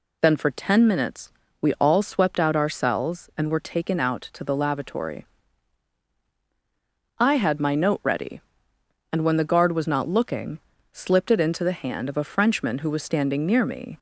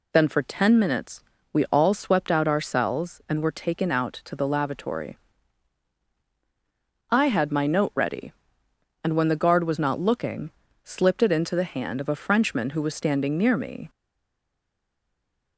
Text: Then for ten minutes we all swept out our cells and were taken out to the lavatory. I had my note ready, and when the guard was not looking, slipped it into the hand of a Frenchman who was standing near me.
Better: first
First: pauses between "minutes" and "we"; slight; at 1.2 s; 0.30 s long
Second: pauses between "minutes" and "we"; slight; at 1.2 s; 0.30 s long // stays silent after the last word; noticeable; from 13.8 s on; 1.7 s long

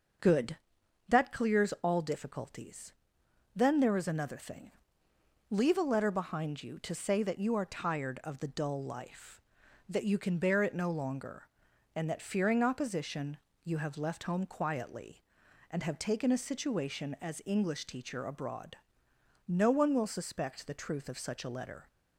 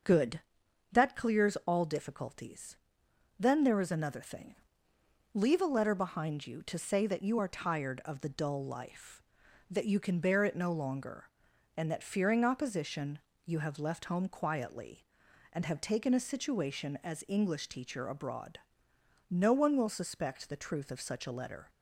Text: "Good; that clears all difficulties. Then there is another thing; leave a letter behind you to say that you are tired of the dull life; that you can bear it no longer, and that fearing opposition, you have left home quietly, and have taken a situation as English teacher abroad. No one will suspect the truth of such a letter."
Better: neither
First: none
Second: none

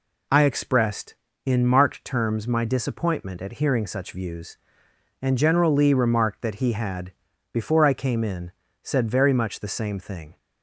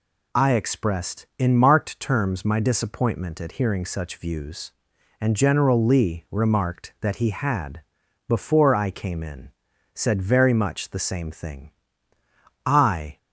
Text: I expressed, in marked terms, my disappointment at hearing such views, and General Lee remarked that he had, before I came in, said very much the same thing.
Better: first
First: none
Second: goes on to say "I"; from 12.6 s on; 0.52 s long

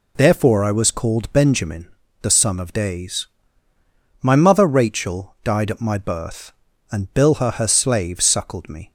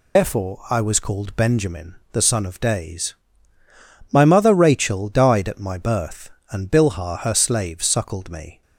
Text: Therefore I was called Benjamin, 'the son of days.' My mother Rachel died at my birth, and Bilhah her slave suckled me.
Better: first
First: none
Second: loses the start of "Therefore"; at 0.1 s; 105 ms

